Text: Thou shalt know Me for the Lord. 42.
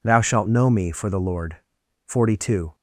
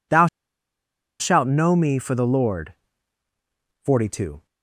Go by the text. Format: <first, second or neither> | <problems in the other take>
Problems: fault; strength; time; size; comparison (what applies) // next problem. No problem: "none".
first | pauses between "Thou" and "shalt"; noticeable; at 0.2 s; 0.93 s long